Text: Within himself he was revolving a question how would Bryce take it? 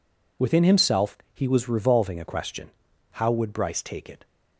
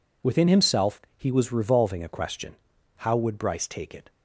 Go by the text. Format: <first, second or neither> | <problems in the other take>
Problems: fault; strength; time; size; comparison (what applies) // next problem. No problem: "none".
neither | pauses between "himself" and "he"; slight; the same in both // pauses between "question" and "how"; the same in both